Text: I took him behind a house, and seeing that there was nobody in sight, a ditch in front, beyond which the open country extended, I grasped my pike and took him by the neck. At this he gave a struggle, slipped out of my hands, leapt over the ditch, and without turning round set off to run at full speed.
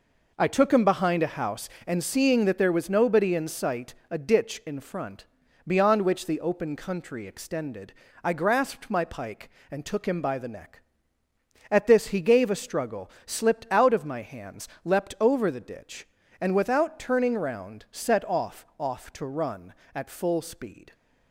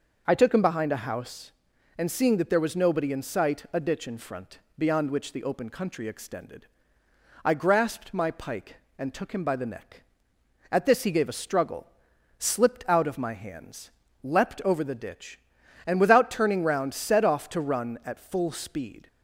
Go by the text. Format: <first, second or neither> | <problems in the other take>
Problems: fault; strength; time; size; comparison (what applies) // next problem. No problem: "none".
second | says "off" twice; at 18.7 s